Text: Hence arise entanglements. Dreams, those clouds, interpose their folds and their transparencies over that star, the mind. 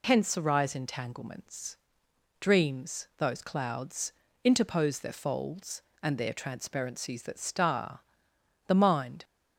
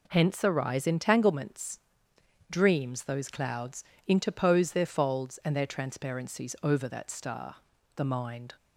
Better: second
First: skips "over"; at 7.2 s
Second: none

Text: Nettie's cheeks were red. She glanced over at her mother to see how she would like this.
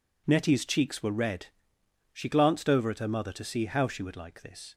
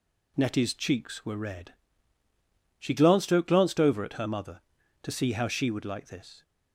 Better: first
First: none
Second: says "glanced" twice; at 3.4 s

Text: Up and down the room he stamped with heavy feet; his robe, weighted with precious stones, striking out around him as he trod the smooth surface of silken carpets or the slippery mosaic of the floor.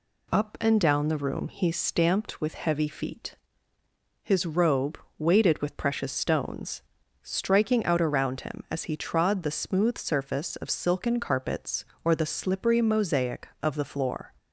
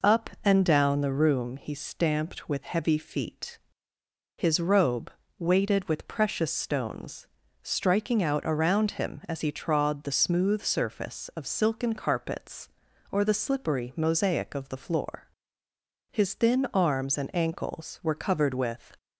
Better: first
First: none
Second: goes on to say "His thin arms and ankles were covered with"; strong; from 16.1 s on; 2.8 s long

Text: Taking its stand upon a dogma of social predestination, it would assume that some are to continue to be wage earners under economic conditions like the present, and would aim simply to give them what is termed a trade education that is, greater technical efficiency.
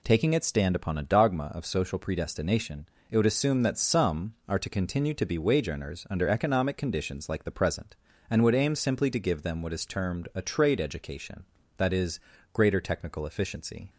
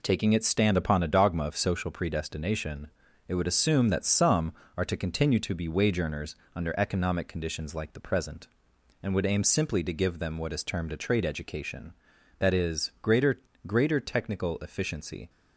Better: first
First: none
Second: pauses between "earners" and "under"; slight; at 6.3 s; 0.20 s long // says "greater" twice; at 13.6 s

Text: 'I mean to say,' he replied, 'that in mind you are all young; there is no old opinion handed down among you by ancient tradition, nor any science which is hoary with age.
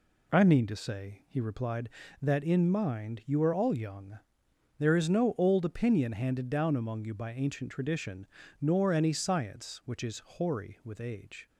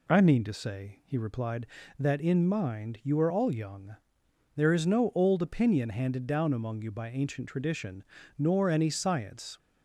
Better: first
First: none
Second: stops before "which is hoary with age"; at 9.5 s

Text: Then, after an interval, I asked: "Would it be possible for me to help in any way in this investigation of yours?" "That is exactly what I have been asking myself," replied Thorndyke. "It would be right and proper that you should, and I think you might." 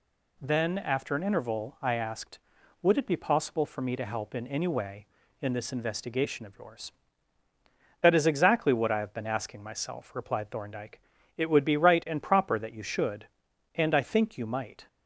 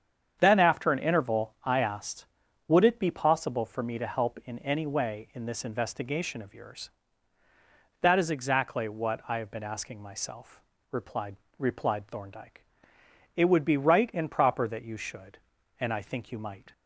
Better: first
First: none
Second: starts louder than the rest; strong; until 1.4 s; 8 dB // says "replied" twice; at 11.5 s

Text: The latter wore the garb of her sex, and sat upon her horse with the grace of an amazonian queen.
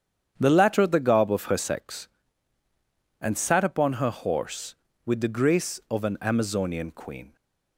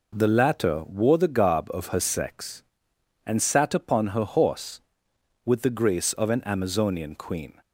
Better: second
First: starts louder than the rest; strong; until 1.3 s; 8.5 dB // skips "wore"; at 0.8 s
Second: none

